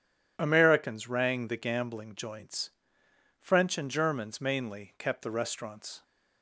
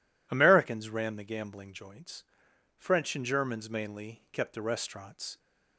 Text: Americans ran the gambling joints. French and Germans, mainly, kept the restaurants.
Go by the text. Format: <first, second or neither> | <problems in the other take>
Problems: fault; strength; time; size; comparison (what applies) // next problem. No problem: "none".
second | says "rang" for "ran"; at 1.0 s